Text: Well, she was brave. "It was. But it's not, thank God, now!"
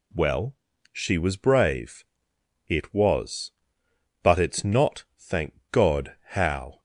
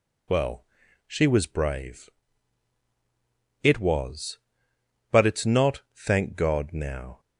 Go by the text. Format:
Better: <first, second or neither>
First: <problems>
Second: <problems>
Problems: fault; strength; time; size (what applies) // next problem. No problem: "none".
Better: second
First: pauses between "thank" and "God"; slight; at 5.5 s; 0.16 s long // says "how" for "now"; at 6.2 s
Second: none